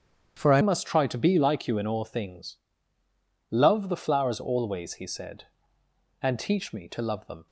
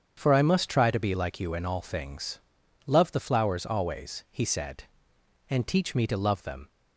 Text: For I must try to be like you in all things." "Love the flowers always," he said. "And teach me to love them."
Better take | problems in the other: second | starts louder than the rest; strong; until 1.3 s; 8.5 dB; strong in the second // changes voice at "must"; from 0.6 s on; 6.8 s long

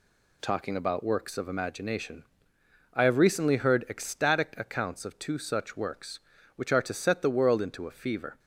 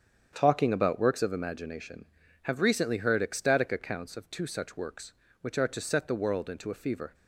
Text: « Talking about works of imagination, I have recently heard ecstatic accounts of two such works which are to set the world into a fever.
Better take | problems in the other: first | starts louder than the rest; strong; until 1.3 s; 8 dB // skips "I"; at 2.2 s

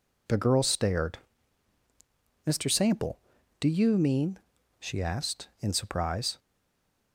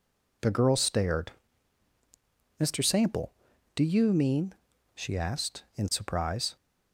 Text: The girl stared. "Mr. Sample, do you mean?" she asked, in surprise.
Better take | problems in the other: second | stays silent after the last word; slight; from 6.3 s on; 0.8 s long

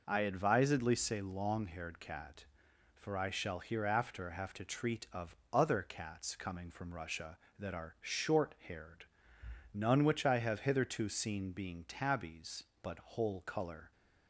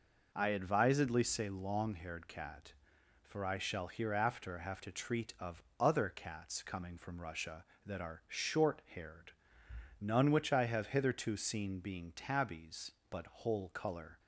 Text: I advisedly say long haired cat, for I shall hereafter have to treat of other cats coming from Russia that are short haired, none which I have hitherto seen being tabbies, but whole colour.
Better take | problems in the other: neither | pauses between "of" and "other"; slight; the same in both

